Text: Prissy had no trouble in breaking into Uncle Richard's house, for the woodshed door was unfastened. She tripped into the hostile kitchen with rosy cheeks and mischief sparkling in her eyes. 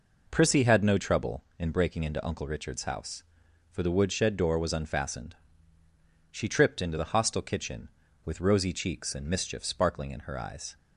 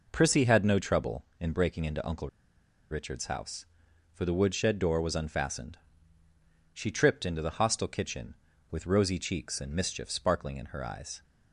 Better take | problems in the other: first | pauses between "Uncle" and "Richard's"; noticeable; at 2.2 s; 0.61 s long

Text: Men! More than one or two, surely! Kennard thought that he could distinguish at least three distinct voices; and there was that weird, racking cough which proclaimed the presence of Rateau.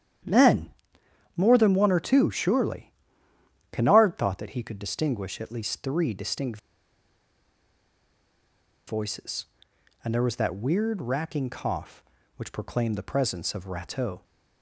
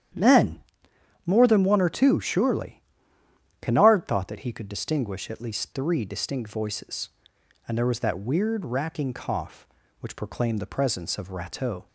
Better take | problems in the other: second | starts louder than the rest; strong; until 1.9 s; 10 dB; strong in the second // pauses between "distinct" and "voices"; strong; at 6.5 s; 2.2 s long

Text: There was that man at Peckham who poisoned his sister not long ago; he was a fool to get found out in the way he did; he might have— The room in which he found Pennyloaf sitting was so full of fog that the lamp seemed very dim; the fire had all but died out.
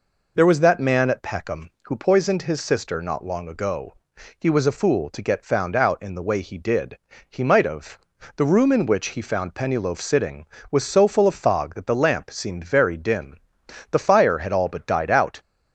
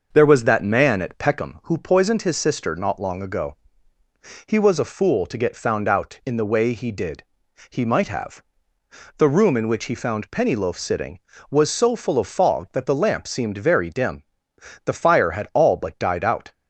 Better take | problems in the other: first | starts louder than the rest; noticeable; until 1.5 s; 6 dB

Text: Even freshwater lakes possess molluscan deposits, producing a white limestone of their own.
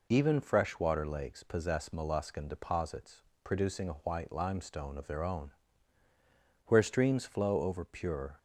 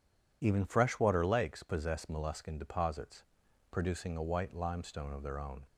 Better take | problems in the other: second | goes on to say "Where streams flow over pure"; strong; from 6.6 s on; 1.7 s long

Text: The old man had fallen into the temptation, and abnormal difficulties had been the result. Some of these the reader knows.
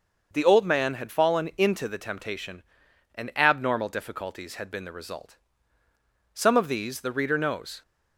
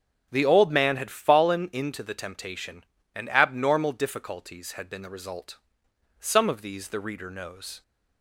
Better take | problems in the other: neither | starts louder than the rest; the same in both

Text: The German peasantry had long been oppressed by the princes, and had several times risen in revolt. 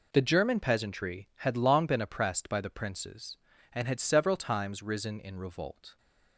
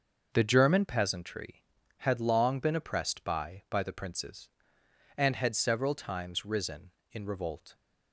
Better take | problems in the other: first | says "by" twice; at 3.6 s

